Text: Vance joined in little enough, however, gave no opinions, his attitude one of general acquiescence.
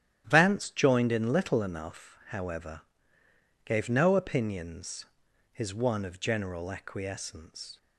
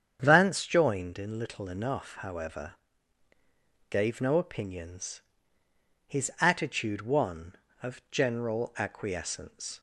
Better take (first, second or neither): second